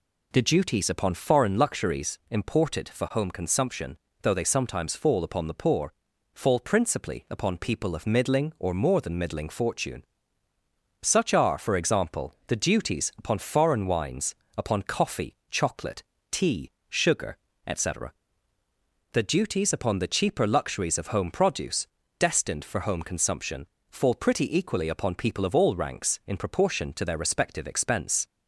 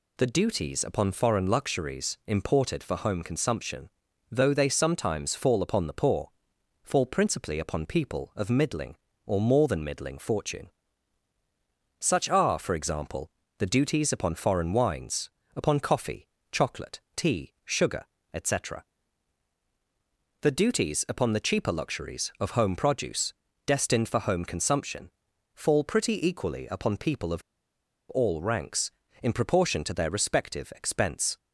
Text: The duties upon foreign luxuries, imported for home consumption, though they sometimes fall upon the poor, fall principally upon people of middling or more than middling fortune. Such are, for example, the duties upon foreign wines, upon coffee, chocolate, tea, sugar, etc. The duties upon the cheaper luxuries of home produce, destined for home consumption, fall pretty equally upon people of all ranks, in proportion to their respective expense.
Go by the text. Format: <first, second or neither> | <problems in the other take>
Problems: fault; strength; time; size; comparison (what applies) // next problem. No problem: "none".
first | pauses between "of" and "all"; noticeable; at 27.4 s; 0.68 s long